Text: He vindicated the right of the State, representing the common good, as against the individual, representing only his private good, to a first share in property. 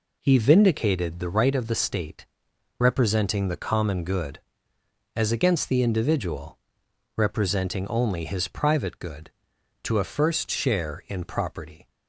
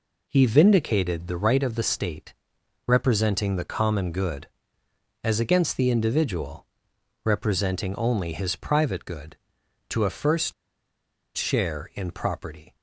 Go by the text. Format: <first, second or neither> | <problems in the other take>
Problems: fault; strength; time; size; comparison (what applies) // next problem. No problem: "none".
first | pauses between "first" and "share"; noticeable; at 10.5 s; 0.81 s long